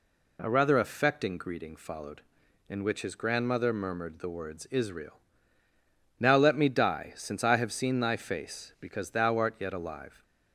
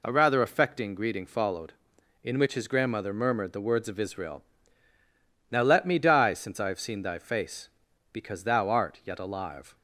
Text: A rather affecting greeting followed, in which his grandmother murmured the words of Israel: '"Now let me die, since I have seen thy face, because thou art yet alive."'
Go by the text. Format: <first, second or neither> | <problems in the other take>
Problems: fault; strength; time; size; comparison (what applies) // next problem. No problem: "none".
second | skips "of"; at 4.6 s